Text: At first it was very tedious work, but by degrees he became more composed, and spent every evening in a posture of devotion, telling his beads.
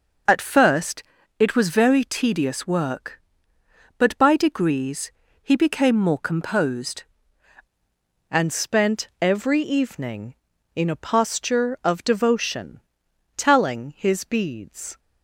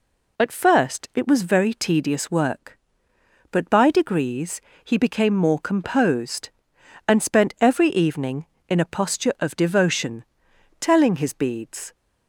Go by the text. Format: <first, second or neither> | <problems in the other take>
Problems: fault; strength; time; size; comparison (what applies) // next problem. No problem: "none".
second | pauses between "first" and "it"; slight; at 1.0 s; 0.36 s long // pauses between "degrees" and "he"; slight; at 5.1 s; 0.28 s long; slight in the second // changes voice at "and"; from 8.2 s on; 6.7 s long